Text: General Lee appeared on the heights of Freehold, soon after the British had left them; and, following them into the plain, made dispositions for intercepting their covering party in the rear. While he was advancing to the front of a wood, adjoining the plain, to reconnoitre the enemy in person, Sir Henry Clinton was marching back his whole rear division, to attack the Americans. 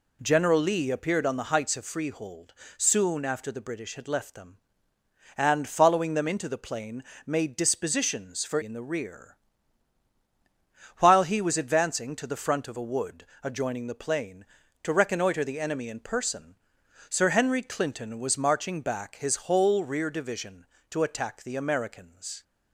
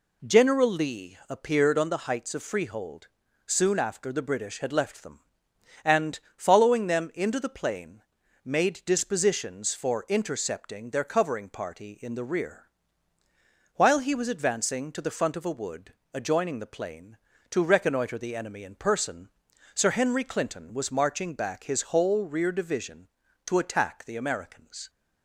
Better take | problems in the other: second | skips "intercepting their covering party"; at 8.6 s

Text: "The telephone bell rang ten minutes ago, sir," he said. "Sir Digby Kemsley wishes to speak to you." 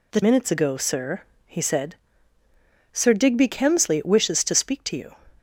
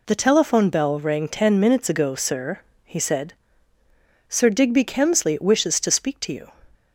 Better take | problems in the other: second | skips "telephone bell rang ten"; at 0.2 s

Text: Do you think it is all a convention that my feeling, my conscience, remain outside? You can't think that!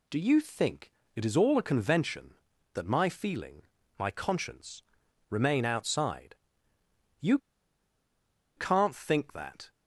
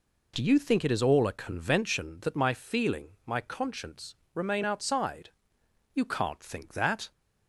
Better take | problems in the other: second | pauses between "think" and "it"; slight; at 0.9 s; 0.24 s long // pauses between "You" and "can't"; at 7.3 s; 1.1 s long

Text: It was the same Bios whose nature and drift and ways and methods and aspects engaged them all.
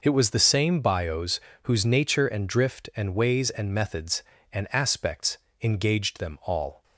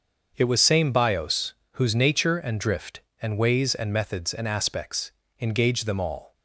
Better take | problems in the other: first | starts louder than the rest; until 1.3 s; 6.5 dB // skips "the"; at 0.5 s // pauses between "Bios" and "whose"; slight; at 1.5 s; 0.20 s long; slight in the first // pauses between "aspects" and "engaged"; slight; at 5.1 s; 0.28 s long; slight in the first

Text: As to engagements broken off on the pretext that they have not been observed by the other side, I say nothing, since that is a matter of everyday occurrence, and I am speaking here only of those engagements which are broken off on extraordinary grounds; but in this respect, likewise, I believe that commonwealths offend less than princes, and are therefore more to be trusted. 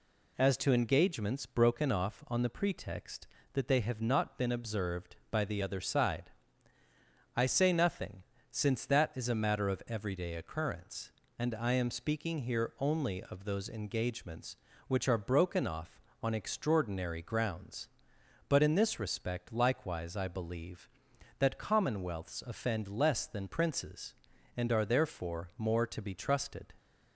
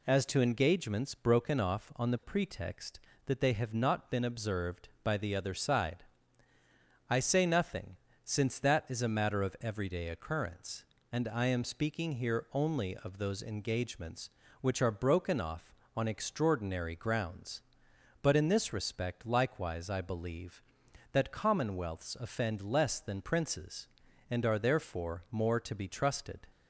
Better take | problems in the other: neither | none

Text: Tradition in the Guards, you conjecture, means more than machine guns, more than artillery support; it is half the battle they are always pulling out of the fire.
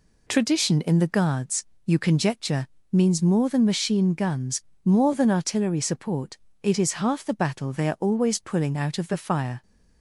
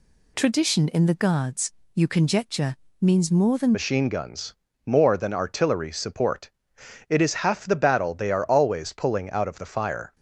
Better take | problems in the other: first | changes voice at "machine"; from 3.7 s on; 6.4 s long

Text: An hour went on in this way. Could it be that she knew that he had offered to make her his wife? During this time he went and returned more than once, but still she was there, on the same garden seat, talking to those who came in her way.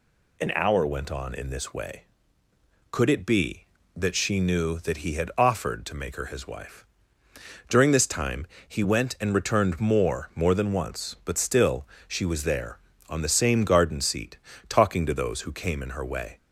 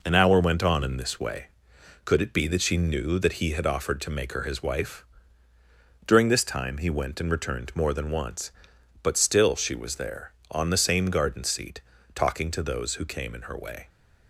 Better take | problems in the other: second | pauses between "time" and "he"; slight; at 8.4 s; 0.22 s long // says "more" twice; at 10.3 s // pauses between "still" and "she"; slight; at 11.8 s; 0.22 s long

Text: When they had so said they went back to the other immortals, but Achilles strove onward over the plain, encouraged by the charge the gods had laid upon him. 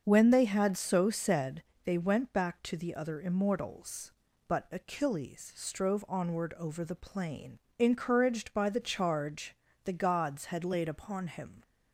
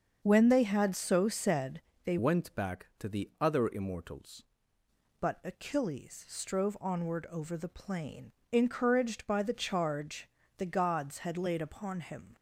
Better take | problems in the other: first | starts louder than the rest; until 1.2 s; 7 dB; also in the first // pauses between "said" and "they"; slight; at 1.8 s; 0.24 s long; slight in the first // changes voice from "went" to "immortals"; from 2.1 to 4.4 s; 2.3 s long // pauses between "charge" and "the"; slight; at 10.2 s; 0.30 s long; slight in the first

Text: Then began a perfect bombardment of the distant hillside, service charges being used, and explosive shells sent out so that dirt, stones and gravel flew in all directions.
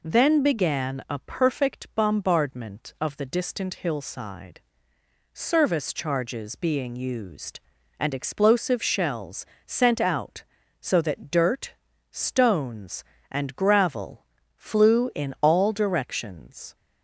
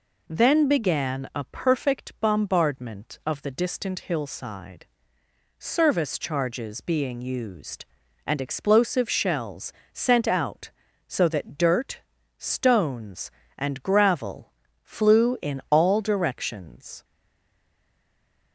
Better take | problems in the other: first | pauses between "shells" and "sent"; slight; at 9.7 s; 0.20 s long; slight in the first // pauses between "gravel" and "flew"; slight; at 14.5 s; 0.30 s long; slight in the first // stays silent after the last word; noticeable; from 17.0 s on; 1.5 s long

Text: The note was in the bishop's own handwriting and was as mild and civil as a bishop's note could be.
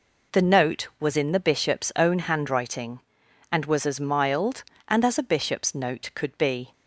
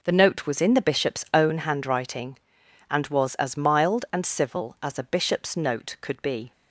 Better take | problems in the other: second | skips "civil"; at 5.0 s

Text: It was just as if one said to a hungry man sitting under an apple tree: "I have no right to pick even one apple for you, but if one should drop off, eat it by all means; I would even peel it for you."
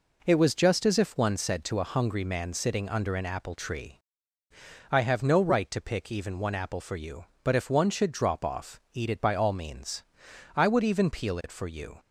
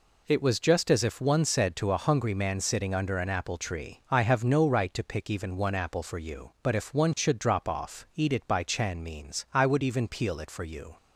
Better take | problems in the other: first | says "chan" for "all"; at 8.6 s

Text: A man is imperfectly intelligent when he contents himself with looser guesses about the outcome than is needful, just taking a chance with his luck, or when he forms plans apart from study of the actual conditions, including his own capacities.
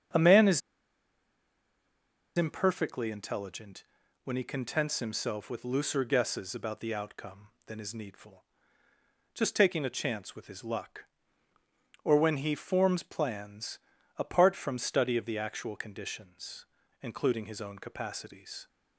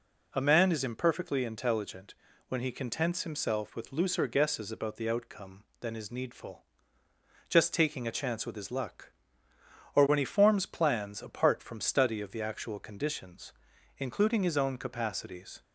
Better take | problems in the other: second | starts louder than the rest; strong; until 2.9 s; 7.5 dB // pauses between "is" and "imperfectly"; strong; at 0.6 s; 1.7 s long // pauses between "intelligent" and "when"; at 3.8 s; 0.40 s long; slight in the second // pauses between "plans" and "apart"; at 13.7 s; 0.38 s long

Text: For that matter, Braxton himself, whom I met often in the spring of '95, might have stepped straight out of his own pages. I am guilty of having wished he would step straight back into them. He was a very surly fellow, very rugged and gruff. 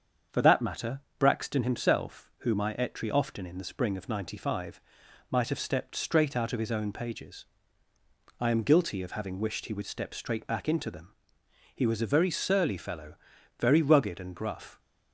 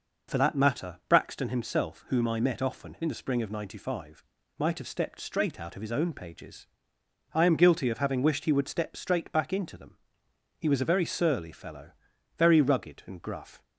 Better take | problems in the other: second | starts louder than the rest; until 1.5 s; 7 dB // says "etry" for "met"; at 2.7 s

